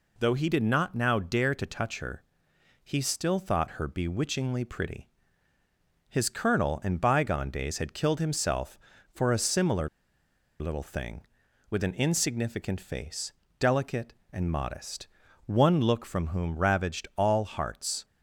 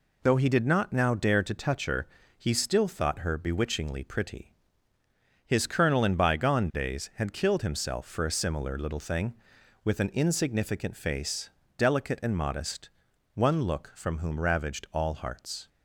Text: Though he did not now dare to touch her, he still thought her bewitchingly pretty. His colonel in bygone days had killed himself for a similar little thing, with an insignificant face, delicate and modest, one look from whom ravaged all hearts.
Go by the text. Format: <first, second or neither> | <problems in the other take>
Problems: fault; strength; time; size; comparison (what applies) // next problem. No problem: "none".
second | pauses between "similar" and "little"; noticeable; at 9.8 s; 0.71 s long